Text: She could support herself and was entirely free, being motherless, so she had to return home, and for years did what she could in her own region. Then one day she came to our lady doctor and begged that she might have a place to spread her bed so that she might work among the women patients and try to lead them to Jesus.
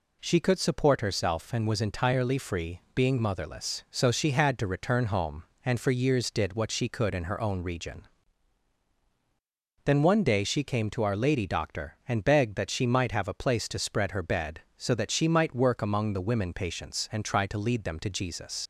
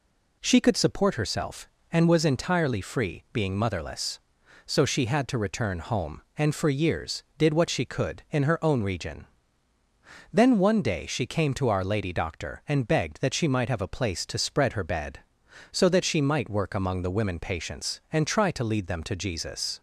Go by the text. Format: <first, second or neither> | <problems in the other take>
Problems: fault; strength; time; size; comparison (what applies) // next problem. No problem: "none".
second | leaves "Jesus" unfinished; at 18.6 s; 75 ms